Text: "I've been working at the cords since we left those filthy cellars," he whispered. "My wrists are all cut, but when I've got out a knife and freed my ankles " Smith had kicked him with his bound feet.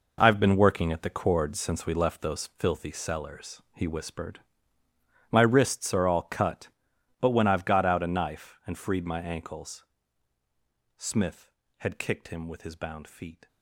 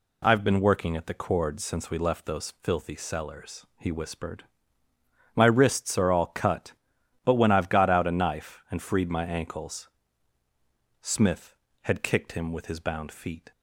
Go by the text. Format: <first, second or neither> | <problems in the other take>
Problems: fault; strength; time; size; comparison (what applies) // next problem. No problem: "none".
second | gets quieter; strong; throughout; 19 dB